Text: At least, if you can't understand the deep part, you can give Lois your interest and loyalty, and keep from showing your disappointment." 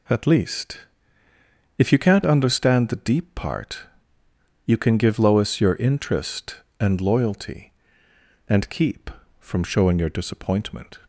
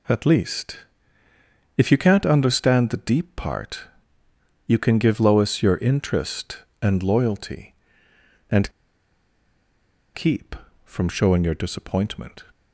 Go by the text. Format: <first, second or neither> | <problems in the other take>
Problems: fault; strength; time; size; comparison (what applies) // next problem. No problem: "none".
first | pauses between "and" and "keep"; strong; at 8.7 s; 1.4 s long